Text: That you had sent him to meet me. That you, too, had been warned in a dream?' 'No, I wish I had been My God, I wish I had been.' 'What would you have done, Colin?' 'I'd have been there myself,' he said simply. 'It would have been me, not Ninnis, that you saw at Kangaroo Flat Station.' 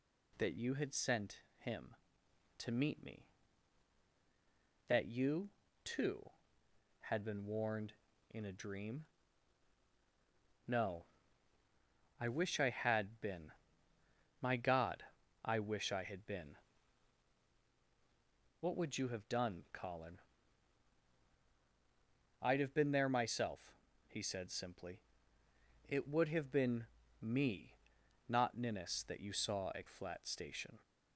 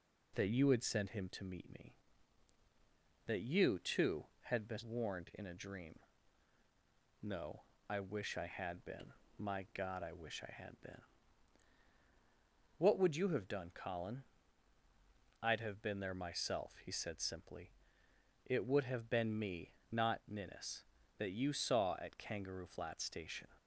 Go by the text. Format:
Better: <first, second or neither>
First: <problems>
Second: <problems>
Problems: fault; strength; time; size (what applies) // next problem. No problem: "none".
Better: second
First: pauses between "sent" and "him"; slight; at 1.4 s; 0.18 s long // pauses between "been" and "My"; noticeable; at 13.5 s; 0.88 s long // pauses between "been" and "me"; slight; at 26.8 s; 0.36 s long // skips "Kangaroo"; at 29.8 s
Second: pauses between "been" and "My"; slight; at 9.1 s; 0.26 s long